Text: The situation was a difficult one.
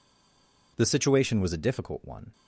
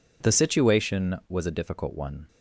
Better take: second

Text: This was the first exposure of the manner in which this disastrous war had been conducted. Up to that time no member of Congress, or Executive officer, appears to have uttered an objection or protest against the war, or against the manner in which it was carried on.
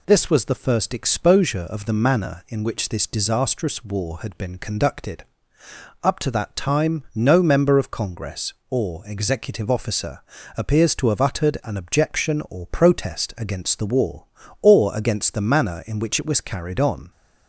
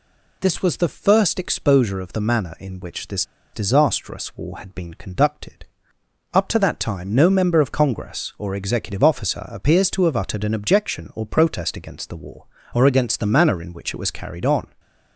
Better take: first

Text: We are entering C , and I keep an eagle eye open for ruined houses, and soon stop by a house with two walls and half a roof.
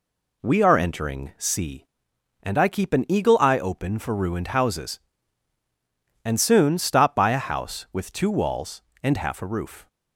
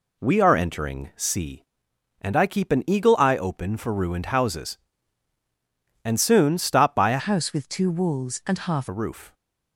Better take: first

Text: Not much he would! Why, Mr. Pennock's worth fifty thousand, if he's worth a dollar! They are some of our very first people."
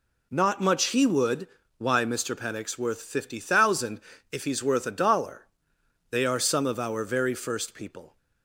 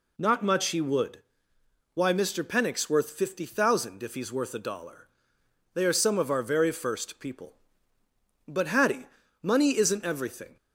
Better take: first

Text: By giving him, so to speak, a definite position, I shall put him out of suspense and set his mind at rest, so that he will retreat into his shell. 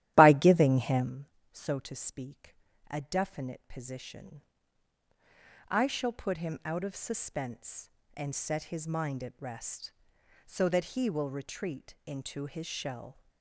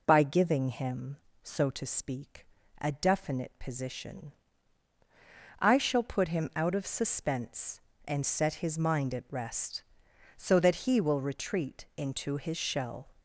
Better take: second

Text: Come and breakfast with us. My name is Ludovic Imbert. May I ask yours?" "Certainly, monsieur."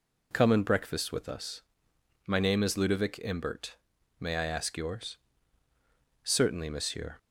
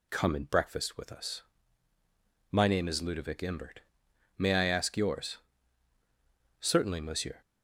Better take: neither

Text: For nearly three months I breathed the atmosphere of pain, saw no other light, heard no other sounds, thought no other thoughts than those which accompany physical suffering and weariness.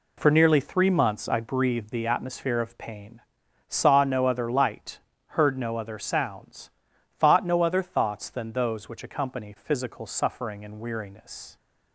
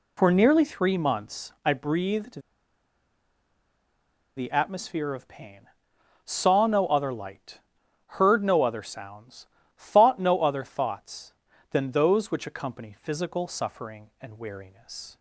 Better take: first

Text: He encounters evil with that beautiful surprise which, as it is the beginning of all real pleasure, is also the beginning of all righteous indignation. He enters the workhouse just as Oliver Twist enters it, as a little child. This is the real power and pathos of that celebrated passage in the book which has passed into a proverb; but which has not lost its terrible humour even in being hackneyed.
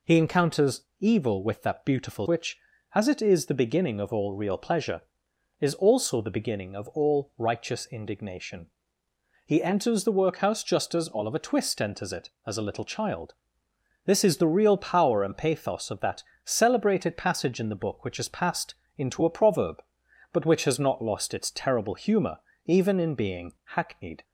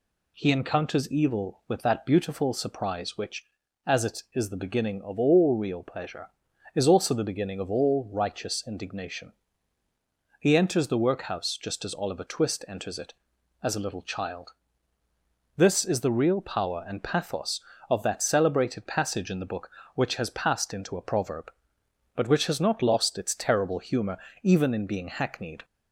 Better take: second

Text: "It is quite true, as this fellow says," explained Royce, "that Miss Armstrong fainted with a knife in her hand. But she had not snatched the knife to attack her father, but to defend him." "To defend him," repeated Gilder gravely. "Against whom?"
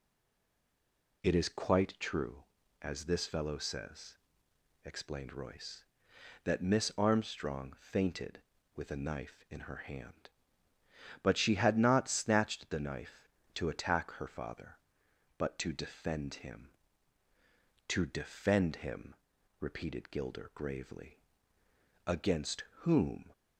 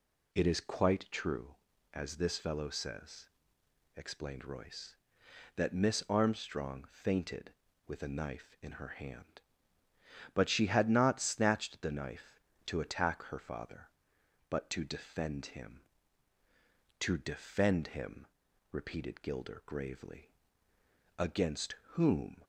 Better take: second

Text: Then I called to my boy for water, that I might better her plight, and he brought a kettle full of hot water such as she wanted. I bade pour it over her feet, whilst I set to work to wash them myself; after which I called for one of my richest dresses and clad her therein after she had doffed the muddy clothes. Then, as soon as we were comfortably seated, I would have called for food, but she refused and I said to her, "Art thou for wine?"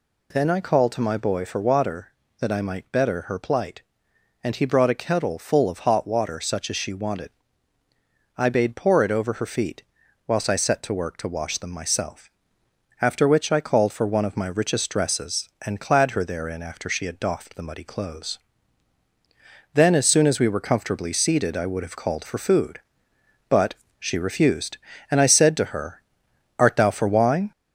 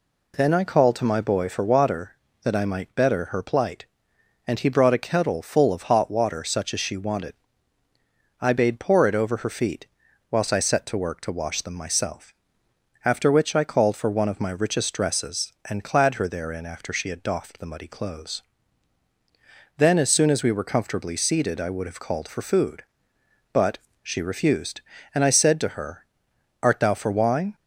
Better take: second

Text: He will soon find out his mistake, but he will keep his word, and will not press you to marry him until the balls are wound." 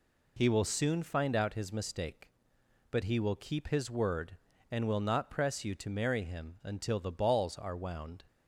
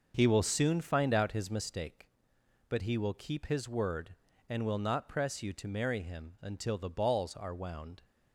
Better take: first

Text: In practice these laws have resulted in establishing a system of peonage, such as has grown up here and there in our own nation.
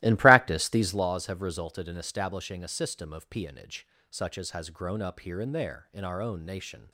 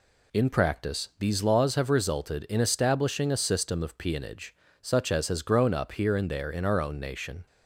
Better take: second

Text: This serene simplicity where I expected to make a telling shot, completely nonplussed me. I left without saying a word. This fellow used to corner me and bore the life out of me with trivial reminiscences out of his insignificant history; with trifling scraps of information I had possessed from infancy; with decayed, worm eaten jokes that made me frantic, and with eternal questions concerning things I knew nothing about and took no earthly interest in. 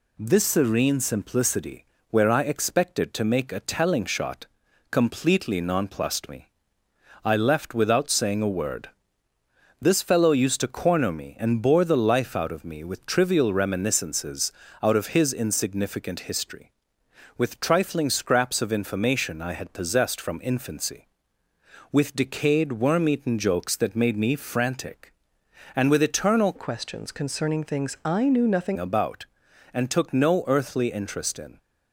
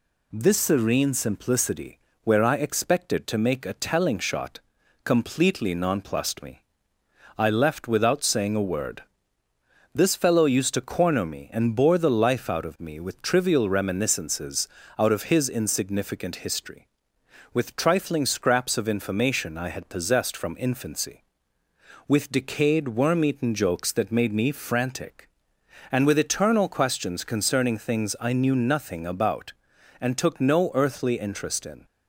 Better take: second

